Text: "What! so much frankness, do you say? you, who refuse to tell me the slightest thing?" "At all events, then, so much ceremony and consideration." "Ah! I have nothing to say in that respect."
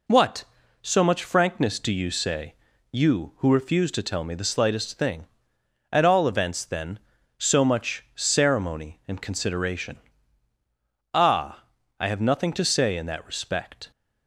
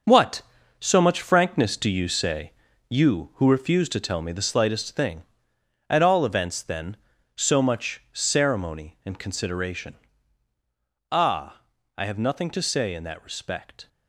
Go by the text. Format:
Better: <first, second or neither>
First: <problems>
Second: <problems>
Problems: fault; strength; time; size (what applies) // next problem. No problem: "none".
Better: first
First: none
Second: gets quieter; strong; throughout; 9 dB